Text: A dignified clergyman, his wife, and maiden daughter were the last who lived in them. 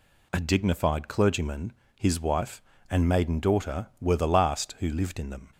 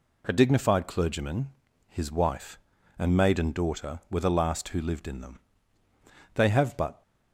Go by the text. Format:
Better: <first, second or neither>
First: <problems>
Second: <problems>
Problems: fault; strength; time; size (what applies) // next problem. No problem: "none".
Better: first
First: none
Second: goes on to say "They have but"; noticeable; from 6.3 s on; 0.68 s long